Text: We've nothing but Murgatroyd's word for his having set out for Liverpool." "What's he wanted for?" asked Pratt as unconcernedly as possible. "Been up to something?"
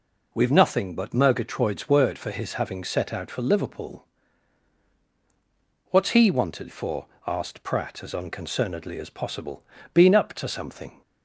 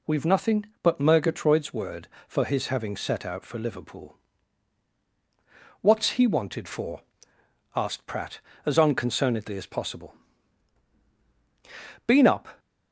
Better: first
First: none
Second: stops before "to something"; at 12.5 s

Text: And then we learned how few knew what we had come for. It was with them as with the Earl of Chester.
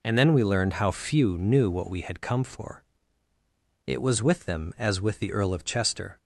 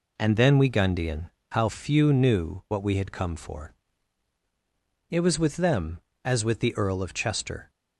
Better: first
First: none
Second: says "gundian" for "learned"; at 0.6 s

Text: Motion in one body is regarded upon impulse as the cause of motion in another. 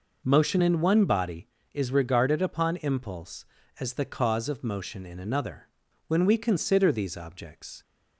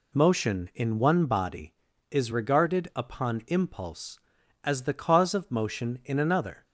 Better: second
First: goes on to say "When we consider these objects"; strong; from 6.0 s on; 1.7 s long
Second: none

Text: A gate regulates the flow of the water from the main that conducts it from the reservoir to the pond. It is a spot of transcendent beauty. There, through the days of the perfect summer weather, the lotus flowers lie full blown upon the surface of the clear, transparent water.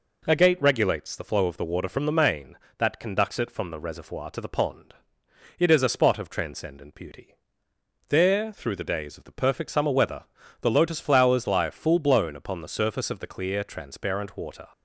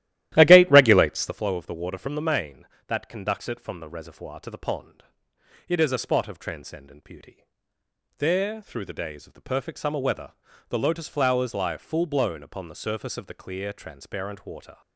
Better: first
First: none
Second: starts louder than the rest; strong; until 1.4 s; 14 dB

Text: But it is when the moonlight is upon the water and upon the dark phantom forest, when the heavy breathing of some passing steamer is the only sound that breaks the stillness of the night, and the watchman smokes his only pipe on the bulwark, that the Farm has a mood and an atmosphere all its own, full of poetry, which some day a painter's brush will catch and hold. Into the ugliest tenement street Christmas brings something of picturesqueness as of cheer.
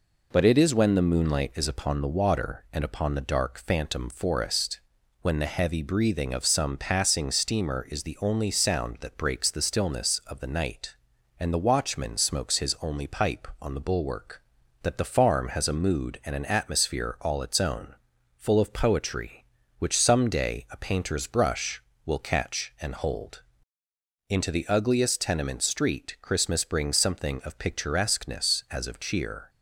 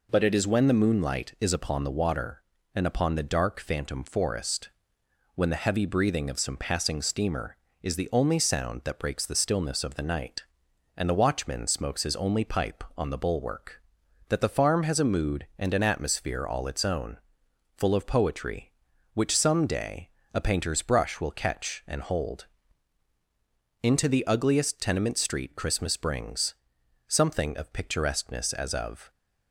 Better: first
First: none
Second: pauses between "day" and "a"; slight; at 20.1 s; 0.24 s long // pauses between "brings" and "something"; noticeable; at 26.5 s; 0.54 s long // stops before "cheer"; at 29.1 s

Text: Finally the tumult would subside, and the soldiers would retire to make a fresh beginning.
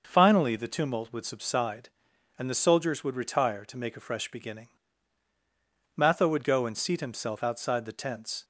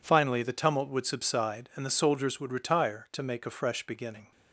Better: second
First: starts louder than the rest; noticeable; until 1.0 s; 6 dB // goes on to say "Matho would go and seat himself outside the tents"; strong; from 5.9 s on; 2.4 s long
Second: none

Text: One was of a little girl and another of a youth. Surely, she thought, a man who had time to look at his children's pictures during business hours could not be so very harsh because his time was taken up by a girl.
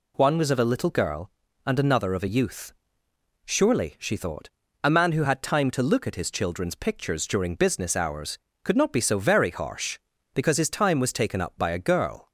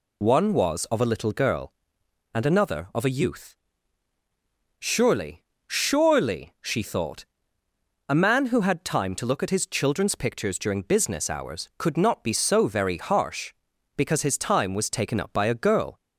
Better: first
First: none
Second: says "Surely" twice; at 5.6 s

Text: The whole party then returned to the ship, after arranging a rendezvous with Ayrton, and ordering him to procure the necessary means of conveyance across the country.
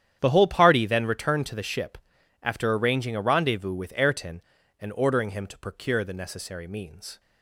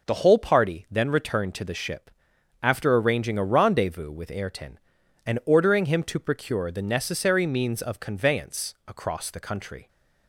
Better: second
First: starts louder than the rest; strong; until 1.2 s; 9.5 dB // stops before "of conveyance across the country"; at 7.1 s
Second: none

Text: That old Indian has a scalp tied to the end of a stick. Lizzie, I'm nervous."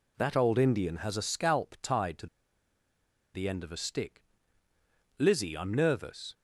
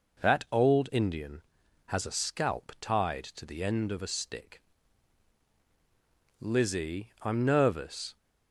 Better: second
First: pauses between "to" and "the"; at 2.2 s; 1.0 s long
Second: none

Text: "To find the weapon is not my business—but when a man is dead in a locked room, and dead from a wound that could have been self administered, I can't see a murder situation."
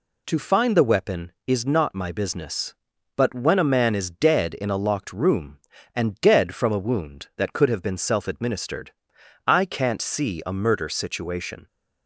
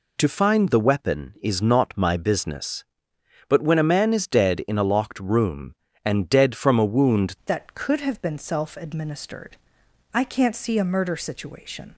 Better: first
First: none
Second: changes voice at "that"; from 7.4 s on; 4.5 s long

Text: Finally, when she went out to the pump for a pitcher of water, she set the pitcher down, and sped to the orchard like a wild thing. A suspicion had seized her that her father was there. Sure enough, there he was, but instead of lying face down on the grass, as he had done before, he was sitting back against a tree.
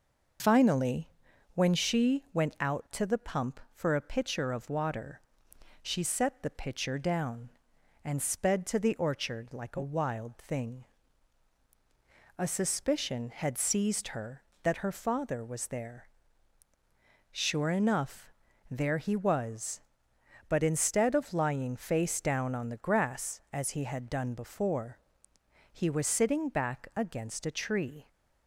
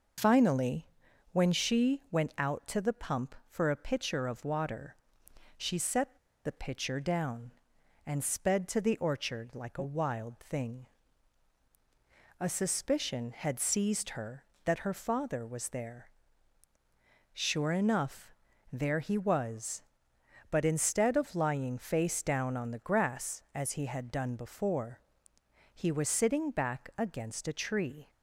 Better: first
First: none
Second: pauses between "set" and "the"; slight; at 6.1 s; 0.28 s long

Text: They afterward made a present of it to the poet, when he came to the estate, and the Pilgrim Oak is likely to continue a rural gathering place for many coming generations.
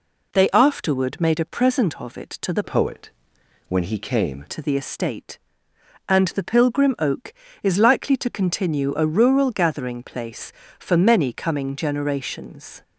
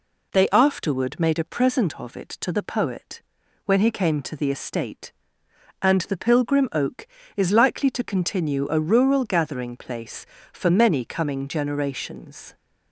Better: second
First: changes voice from "poet" to "came"; from 2.6 to 4.4 s; 1.8 s long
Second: none

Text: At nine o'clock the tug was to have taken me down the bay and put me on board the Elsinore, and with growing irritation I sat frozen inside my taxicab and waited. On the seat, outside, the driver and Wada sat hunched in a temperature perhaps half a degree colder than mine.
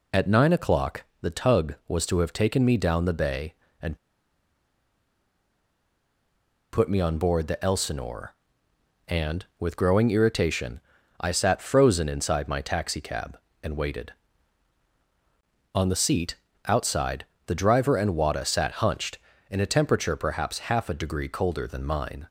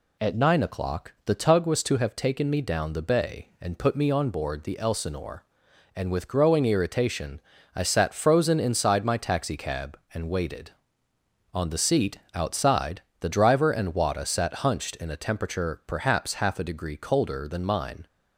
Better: second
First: pauses between "o'clock" and "the"; slight; at 1.0 s; 0.18 s long // pauses between "and" and "put"; strong; at 3.9 s; 2.7 s long // pauses between "irritation" and "I"; at 10.8 s; 0.40 s long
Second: pauses between "irritation" and "I"; slight; at 7.3 s; 0.36 s long

